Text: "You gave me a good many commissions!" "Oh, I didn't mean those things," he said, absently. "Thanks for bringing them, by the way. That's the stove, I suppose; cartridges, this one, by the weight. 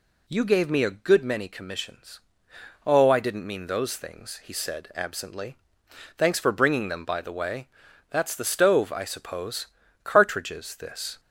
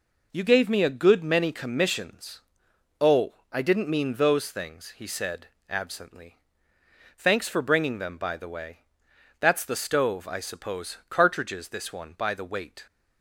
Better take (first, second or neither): second